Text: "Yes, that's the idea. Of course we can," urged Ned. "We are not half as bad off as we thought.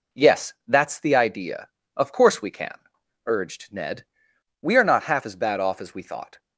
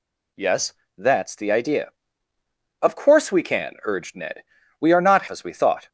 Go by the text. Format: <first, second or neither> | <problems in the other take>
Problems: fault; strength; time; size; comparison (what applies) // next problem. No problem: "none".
first | skips "half as bad off"; at 5.2 s